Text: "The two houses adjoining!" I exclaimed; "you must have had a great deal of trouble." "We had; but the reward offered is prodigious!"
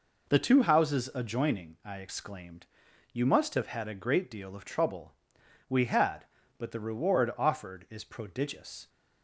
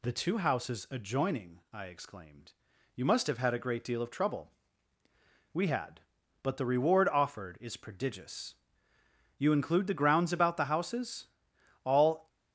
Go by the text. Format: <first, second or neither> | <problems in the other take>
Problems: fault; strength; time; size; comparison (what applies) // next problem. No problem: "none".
first | goes on to say "You include the grounds about the houses All"; strong; from 9.3 s on; 2.9 s long